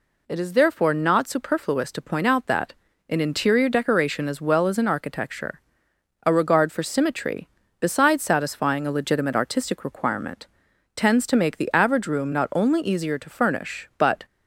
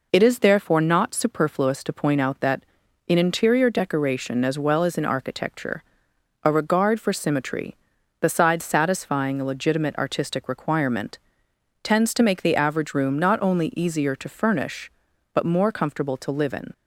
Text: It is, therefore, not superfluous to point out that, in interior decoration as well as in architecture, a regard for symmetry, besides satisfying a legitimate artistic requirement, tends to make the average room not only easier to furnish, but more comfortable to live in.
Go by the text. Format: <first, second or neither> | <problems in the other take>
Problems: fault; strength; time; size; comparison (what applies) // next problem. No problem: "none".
second | stops before "more comfortable to live in"; at 14.2 s